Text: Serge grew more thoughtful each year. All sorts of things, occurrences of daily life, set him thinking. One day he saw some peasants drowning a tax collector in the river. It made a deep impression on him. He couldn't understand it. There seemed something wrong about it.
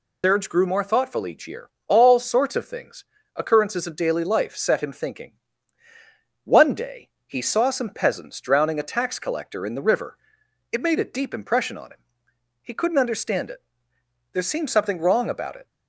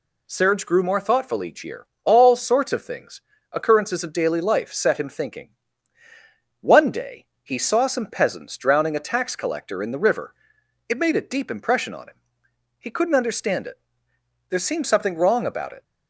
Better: second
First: loses the start of "Serge"; at 0.2 s; 140 ms // pauses between "day" and "he"; slight; at 7.0 s; 0.16 s long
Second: pauses between "day" and "he"; slight; at 7.2 s; 0.16 s long

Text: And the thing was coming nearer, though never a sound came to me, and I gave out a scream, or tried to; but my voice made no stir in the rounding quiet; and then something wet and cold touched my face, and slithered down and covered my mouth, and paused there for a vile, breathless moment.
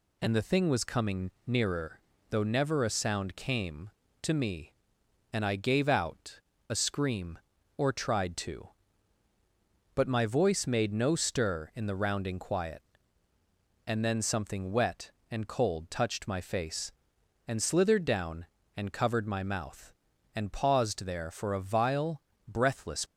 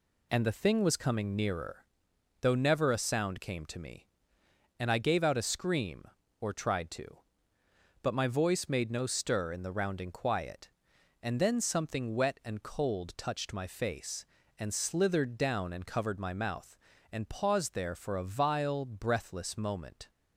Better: second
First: pauses between "out" and "a"; slight; at 6.3 s; 0.30 s long // stops before "moment"; at 23.0 s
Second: none

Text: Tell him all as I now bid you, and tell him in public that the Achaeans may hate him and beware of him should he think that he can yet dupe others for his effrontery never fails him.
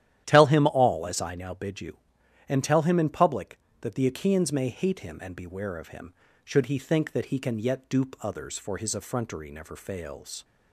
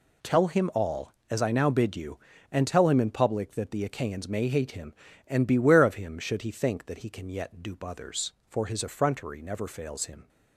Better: second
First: starts louder than the rest; strong; until 1.2 s; 11.5 dB // stops before "him"; at 10.4 s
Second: none

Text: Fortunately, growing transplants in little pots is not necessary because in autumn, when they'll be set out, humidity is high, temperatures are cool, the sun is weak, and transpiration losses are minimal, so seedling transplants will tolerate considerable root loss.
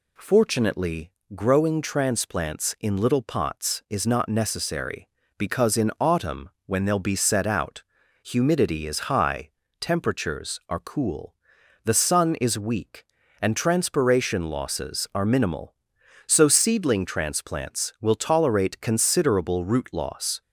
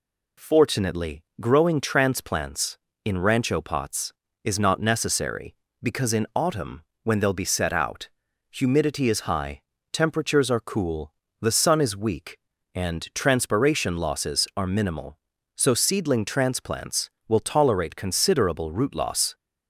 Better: first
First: none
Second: says "rancho" for "little"; at 3.1 s

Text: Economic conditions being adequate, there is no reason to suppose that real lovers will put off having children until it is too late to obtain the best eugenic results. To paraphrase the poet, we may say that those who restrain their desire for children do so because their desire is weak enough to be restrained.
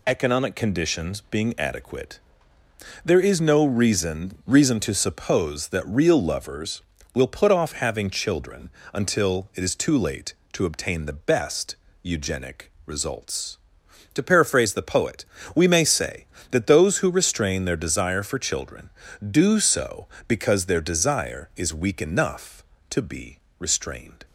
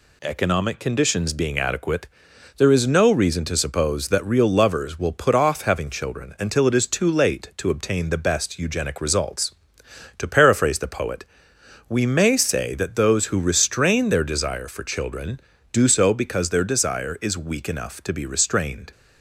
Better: second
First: says "reason" twice; at 4.4 s // pauses between "children" and "until"; slight; at 8.6 s; 0.22 s long // pauses between "best" and "eugenic"; slight; at 11.7 s; 0.26 s long // pauses between "be" and "restrained"; slight; at 23.3 s; 0.22 s long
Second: none

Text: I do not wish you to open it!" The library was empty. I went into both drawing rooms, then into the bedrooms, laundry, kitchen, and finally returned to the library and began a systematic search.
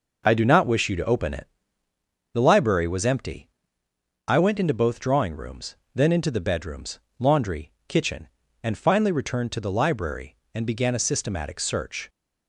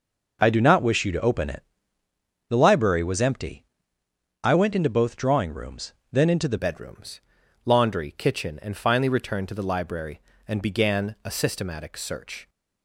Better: first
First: none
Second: changes voice at "bedrooms"; from 6.5 s on; 5.9 s long

